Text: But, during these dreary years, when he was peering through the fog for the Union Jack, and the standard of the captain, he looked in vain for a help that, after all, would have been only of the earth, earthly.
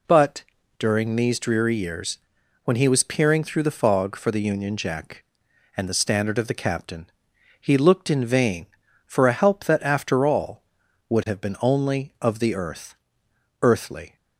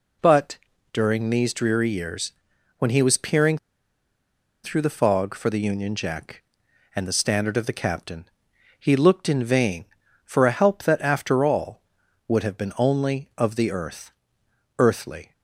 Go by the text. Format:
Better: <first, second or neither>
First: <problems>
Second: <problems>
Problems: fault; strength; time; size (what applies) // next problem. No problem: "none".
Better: first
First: none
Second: pauses between "peering" and "through"; at 3.5 s; 1.0 s long